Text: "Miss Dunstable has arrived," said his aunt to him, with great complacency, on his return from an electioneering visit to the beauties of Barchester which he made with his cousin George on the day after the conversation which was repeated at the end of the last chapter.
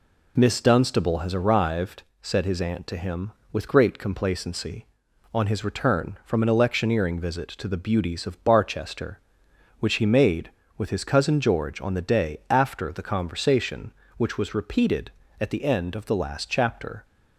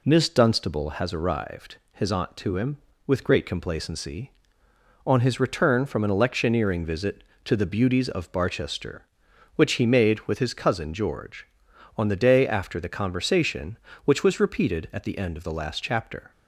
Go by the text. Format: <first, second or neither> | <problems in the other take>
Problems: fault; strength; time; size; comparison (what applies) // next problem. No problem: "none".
first | skips "said"; at 1.8 s